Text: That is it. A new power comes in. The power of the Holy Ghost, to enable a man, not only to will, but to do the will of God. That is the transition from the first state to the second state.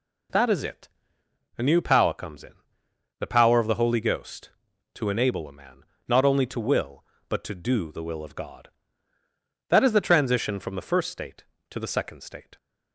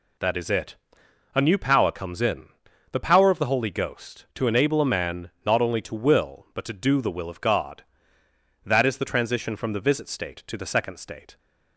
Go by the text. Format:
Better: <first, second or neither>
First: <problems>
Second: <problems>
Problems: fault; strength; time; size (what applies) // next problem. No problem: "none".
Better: first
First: none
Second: says "visit" for "first"; at 9.7 s